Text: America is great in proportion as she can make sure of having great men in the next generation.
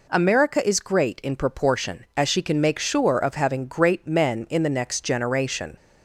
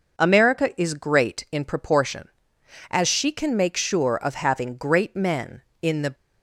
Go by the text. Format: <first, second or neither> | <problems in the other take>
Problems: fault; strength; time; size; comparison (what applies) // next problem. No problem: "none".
first | stops before "next generation"; at 6.1 s